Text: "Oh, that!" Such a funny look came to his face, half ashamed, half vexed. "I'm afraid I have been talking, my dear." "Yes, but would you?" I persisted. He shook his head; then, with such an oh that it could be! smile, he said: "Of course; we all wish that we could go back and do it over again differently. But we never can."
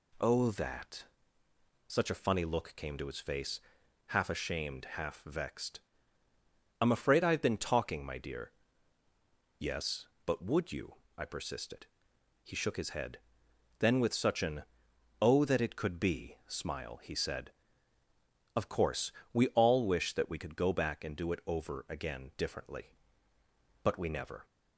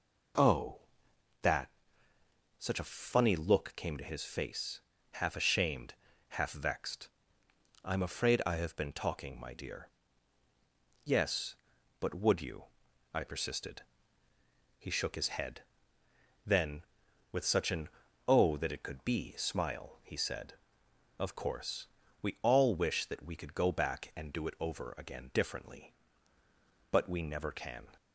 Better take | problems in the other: second | pauses between "an" and "oh"; noticeable; at 14.6 s; 0.54 s long; also in the second // stops before "can"; at 24.4 s

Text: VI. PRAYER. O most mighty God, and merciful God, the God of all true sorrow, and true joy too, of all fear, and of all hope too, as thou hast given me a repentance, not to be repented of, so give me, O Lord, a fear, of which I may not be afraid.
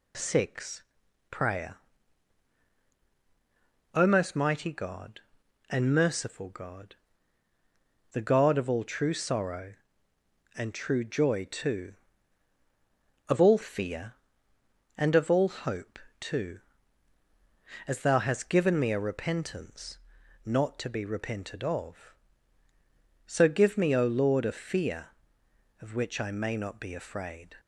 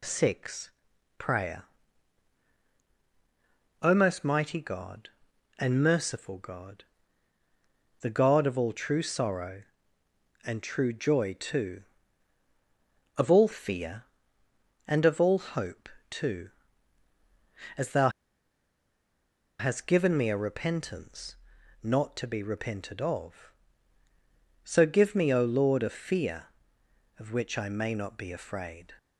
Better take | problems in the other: first | pauses between "hope" and "too"; slight; at 15.8 s; 0.22 s long; slight in the first // pauses between "thou" and "hast"; strong; at 18.0 s; 1.4 s long

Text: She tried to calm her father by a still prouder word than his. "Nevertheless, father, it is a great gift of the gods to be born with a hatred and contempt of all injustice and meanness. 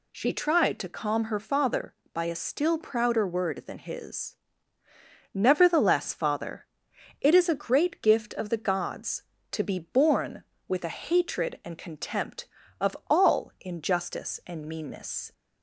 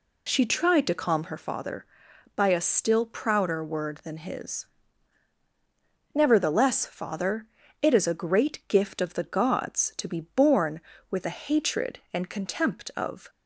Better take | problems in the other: first | stops before "all injustice and meanness"; at 13.2 s

